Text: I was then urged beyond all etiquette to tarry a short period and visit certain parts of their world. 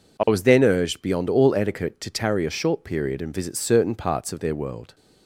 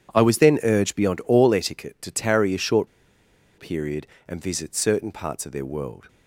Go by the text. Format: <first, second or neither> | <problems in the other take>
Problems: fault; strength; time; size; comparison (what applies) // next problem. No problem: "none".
first | pauses between "short" and "period"; noticeable; at 2.8 s; 0.71 s long